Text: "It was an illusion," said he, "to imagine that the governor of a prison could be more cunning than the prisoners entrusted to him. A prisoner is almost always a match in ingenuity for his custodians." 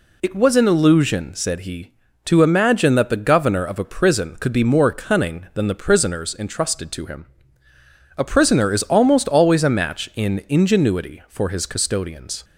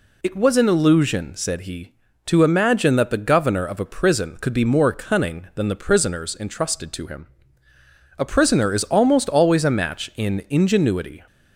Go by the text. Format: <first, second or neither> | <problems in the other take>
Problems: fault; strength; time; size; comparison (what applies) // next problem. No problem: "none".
first | stops before "for his custodians"; at 11.2 s